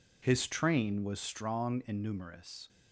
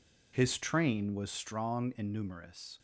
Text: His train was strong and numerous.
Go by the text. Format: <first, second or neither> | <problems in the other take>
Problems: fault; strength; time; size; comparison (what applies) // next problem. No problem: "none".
neither | none